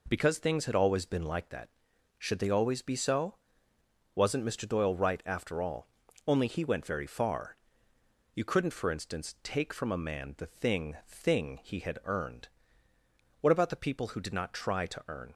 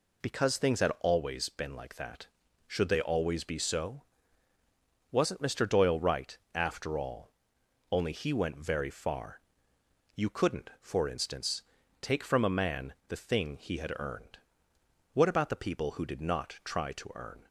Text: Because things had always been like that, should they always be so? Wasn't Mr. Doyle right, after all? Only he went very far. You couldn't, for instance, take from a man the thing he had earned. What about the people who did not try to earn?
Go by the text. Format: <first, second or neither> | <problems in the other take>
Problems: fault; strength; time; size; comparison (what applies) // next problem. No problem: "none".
second | says "thing" twice; at 11.0 s